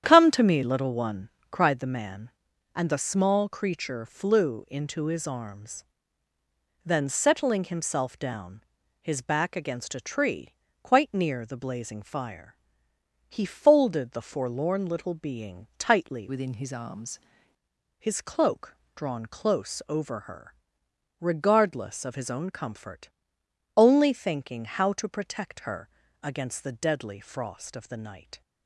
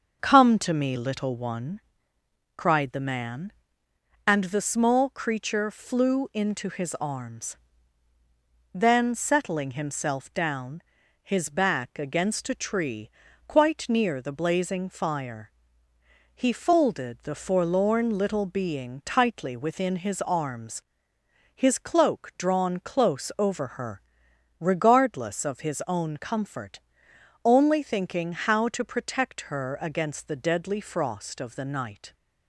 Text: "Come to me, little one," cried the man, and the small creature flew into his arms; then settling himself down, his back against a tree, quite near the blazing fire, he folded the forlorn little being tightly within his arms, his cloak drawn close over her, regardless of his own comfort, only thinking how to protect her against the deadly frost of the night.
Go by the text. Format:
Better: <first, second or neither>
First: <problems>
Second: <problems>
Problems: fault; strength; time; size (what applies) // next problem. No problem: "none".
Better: second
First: starts louder than the rest; strong; until 1.0 s; 10 dB // changes voice from "within" to "arms"; from 16.2 to 17.1 s; 0.9 s long // pauses between "cloak" and "drawn"; slight; at 18.7 s; 0.22 s long // pauses between "her" and "against"; slight; at 25.8 s; 0.34 s long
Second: starts louder than the rest; until 1.2 s; 6.5 dB